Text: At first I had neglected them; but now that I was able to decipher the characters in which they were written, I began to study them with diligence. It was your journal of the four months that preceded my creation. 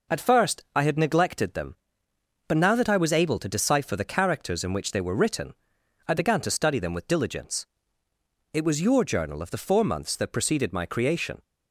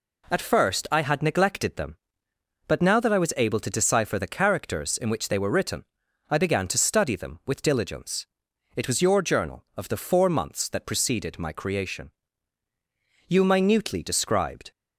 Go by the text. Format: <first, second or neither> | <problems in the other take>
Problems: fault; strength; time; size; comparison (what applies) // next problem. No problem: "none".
first | goes on to say "You minutely described"; from 13.2 s on; 1.4 s long